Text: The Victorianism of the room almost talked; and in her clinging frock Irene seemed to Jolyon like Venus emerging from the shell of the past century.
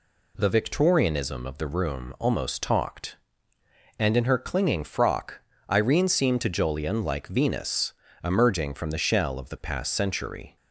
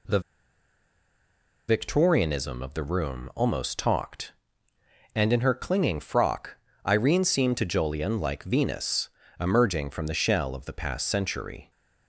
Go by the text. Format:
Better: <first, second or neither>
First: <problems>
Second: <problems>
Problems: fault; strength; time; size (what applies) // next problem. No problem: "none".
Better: first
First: pauses between "frock" and "Irene"; slight; at 5.3 s; 0.32 s long // pauses between "Venus" and "emerging"; slight; at 7.9 s; 0.28 s long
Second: pauses between "The" and "Victorianism"; strong; at 0.1 s; 1.4 s long // pauses between "frock" and "Irene"; slight; at 6.5 s; 0.32 s long // pauses between "Venus" and "emerging"; slight; at 9.0 s; 0.28 s long